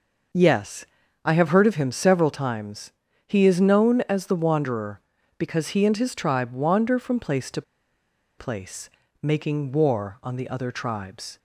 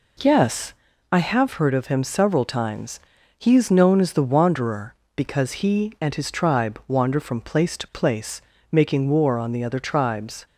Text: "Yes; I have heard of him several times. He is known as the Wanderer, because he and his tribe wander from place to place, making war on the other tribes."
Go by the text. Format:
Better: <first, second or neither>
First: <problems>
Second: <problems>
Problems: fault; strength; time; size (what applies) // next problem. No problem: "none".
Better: second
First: pauses between "to" and "place"; noticeable; at 7.6 s; 0.76 s long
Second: none